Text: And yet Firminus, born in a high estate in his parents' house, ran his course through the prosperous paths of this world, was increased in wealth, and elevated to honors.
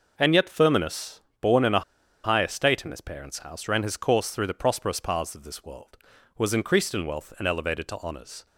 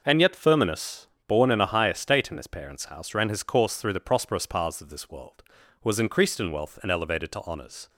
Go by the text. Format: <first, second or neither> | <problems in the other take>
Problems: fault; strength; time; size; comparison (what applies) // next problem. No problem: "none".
second | pauses between "a" and "high"; at 1.8 s; 0.41 s long